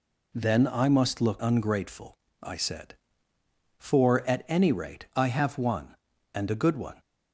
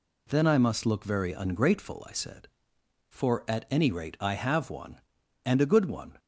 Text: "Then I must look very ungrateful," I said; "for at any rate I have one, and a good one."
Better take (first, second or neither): second